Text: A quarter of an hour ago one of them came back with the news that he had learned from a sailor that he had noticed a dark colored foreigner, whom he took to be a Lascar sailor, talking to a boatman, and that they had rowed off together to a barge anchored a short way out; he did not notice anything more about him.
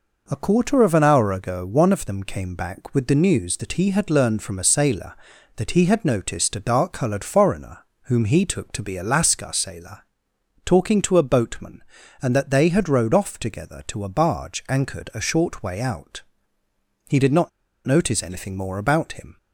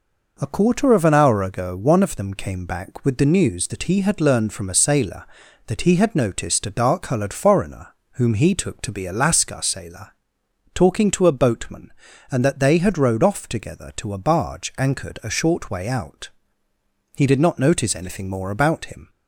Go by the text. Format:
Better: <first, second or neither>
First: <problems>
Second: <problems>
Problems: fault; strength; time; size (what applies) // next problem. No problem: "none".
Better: second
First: pauses between "not" and "notice"; at 17.4 s; 0.37 s long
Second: none